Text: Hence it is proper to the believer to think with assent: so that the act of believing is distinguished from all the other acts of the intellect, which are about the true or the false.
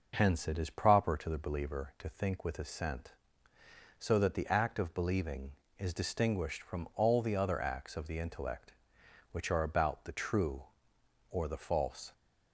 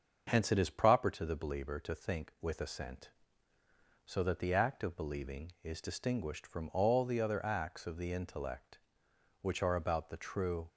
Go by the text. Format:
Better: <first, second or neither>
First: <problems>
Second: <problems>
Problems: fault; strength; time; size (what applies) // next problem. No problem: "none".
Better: first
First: none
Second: starts louder than the rest; until 1.2 s; 6.5 dB // stops before "or the false"; at 10.6 s